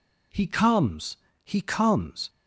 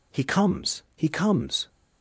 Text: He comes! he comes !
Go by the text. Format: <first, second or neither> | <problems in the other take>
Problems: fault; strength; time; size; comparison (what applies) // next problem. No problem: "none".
neither | none